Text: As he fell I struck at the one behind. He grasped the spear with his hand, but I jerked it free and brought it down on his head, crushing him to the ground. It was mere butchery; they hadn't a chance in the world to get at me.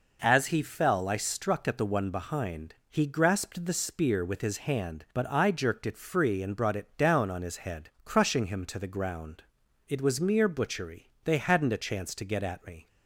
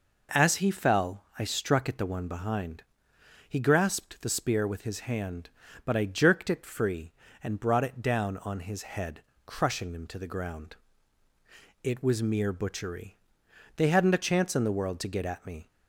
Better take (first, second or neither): second